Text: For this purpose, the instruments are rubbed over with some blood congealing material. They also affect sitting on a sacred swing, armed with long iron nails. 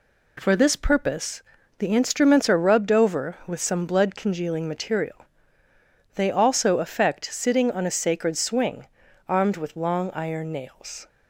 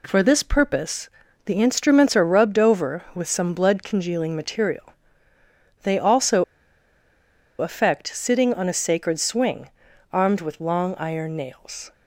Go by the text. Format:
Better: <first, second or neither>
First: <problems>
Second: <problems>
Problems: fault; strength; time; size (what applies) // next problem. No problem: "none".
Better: first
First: none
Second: pauses between "also" and "affect"; at 6.4 s; 1.1 s long